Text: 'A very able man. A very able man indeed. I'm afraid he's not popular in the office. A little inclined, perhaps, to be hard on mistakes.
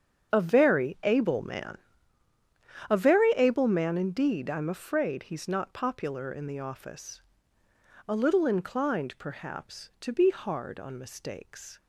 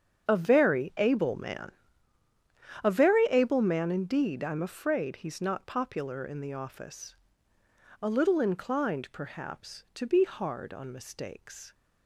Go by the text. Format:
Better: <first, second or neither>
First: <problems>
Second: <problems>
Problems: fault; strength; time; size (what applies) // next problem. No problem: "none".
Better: neither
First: starts louder than the rest; strong; until 1.4 s; 7.5 dB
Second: starts louder than the rest; strong; until 1.3 s; 7.5 dB